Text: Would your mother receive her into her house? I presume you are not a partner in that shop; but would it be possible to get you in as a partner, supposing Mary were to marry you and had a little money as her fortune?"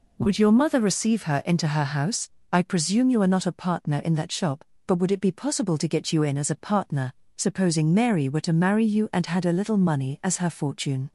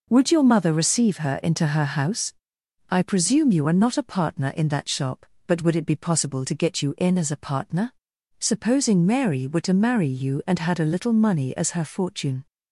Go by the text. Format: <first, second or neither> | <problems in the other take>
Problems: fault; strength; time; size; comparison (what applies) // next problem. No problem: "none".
neither | none